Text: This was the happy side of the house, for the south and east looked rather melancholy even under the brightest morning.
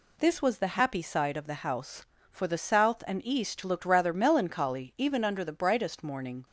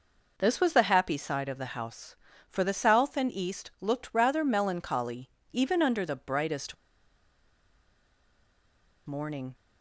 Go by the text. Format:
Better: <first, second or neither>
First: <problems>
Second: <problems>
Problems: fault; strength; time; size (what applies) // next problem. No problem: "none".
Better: first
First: none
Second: pauses between "melancholy" and "even"; slight; at 5.3 s; 0.22 s long // pauses between "brightest" and "morning"; strong; at 6.7 s; 2.3 s long